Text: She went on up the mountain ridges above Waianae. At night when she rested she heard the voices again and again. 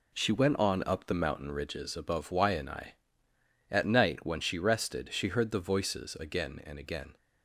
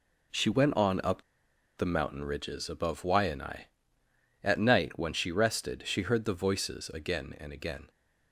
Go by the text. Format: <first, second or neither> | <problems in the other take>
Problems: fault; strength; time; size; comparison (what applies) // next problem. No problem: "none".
first | pauses between "up" and "the"; noticeable; at 1.2 s; 0.55 s long